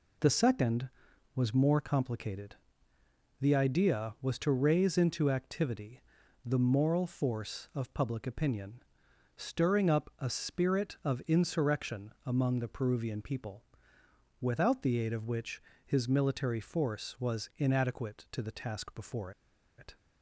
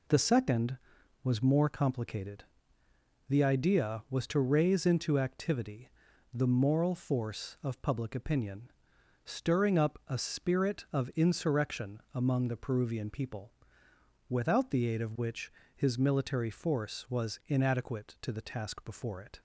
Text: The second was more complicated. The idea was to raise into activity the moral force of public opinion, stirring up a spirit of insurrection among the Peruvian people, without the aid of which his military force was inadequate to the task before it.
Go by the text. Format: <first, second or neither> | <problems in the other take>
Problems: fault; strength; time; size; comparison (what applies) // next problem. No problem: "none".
second | pauses between "activity" and "the"; at 6.0 s; 0.44 s long; also in the second // pauses between "which" and "his"; slight; at 15.6 s; 0.24 s long; slight in the second // pauses between "before" and "it"; noticeable; at 19.3 s; 0.47 s long